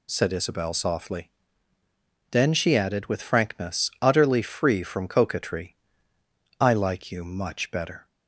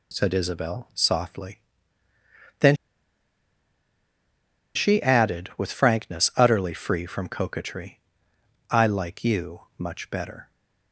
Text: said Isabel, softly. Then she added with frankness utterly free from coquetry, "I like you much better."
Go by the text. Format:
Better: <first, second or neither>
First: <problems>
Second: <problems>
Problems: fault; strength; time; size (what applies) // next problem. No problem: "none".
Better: first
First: none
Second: pauses between "Then" and "she"; strong; at 2.7 s; 2.0 s long // pauses between "you" and "much"; slight; at 9.6 s; 0.16 s long